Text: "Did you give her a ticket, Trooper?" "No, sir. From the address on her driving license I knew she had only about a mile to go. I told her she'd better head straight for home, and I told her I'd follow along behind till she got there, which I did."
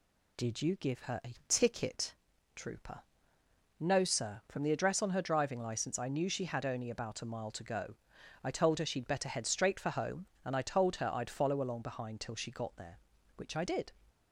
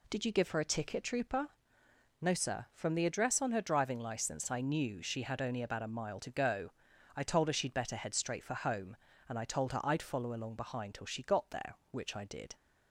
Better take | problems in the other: neither | none

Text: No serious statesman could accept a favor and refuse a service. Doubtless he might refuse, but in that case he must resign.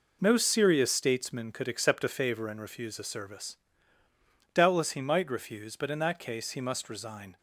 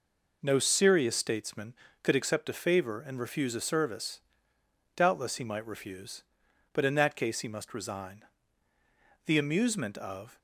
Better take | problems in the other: first | goes on to say "The amusement of"; noticeable; from 9.2 s on; 1.1 s long

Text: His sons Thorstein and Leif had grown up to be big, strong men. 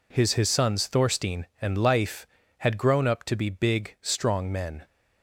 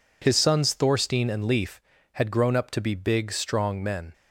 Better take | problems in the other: second | says "His" twice; at 0.3 s

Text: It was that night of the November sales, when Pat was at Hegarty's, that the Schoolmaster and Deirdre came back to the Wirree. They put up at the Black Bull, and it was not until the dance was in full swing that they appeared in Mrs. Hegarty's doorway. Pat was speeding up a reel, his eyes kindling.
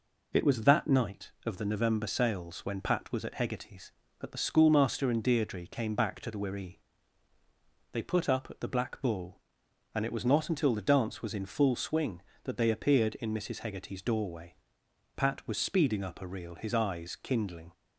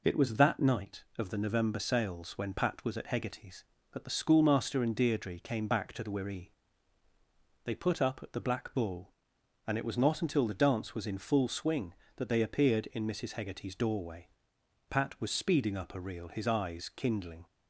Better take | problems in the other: neither | none

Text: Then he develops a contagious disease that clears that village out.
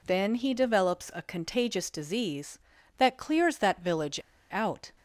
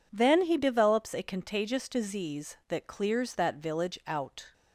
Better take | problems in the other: second | pauses between "village" and "out"; slight; at 4.1 s; 0.34 s long

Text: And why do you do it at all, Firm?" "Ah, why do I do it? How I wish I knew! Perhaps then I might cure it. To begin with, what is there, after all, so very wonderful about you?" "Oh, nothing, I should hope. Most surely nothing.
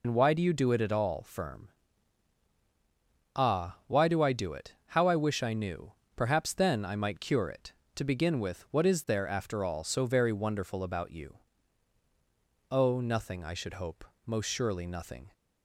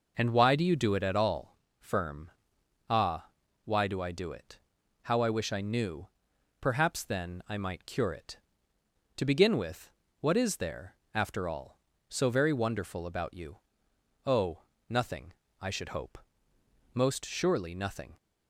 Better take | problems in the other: second | loses the start of "And"; at 0.0 s; 70 ms

